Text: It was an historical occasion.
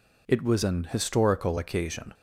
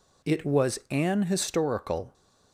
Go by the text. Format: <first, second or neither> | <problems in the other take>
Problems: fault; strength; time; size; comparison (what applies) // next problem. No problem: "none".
first | stops before "occasion"; at 2.1 s